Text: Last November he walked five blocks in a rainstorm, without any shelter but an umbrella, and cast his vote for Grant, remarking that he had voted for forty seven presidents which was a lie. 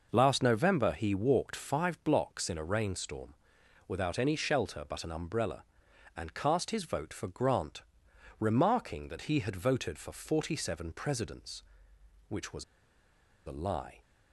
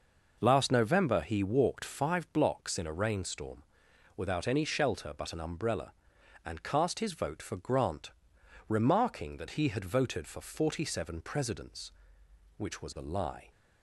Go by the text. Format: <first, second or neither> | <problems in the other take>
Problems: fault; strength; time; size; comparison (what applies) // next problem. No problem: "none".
second | pauses between "was" and "a"; noticeable; at 12.6 s; 0.82 s long